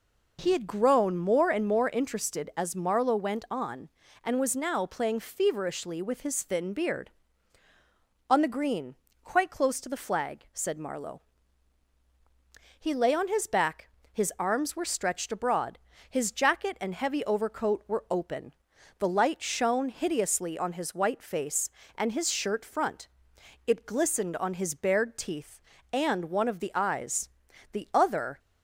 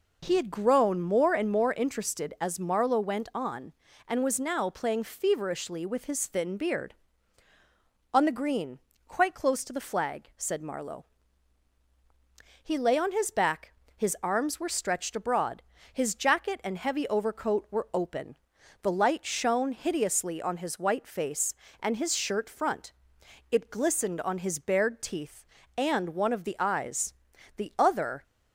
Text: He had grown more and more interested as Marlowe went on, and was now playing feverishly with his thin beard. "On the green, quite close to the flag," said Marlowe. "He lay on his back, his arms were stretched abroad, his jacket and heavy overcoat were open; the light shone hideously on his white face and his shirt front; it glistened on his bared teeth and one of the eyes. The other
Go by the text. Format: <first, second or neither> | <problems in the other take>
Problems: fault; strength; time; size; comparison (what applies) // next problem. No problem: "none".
neither | none